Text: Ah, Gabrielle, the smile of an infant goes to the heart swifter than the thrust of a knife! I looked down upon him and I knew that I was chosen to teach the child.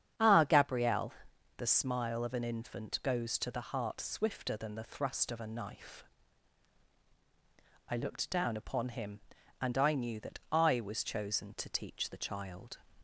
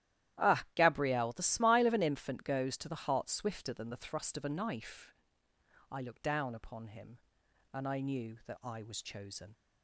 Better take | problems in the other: first | starts louder than the rest; strong; until 1.4 s; 12.5 dB; strong in the first // stops before "to teach the child"; at 9.5 s

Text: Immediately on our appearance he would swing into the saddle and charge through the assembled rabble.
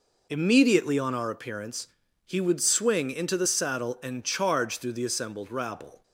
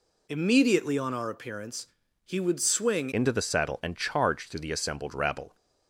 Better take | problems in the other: first | pauses between "appearance" and "he"; at 1.8 s; 0.38 s long; also in the first // changes voice at "into"; from 3.1 s on; 2.4 s long

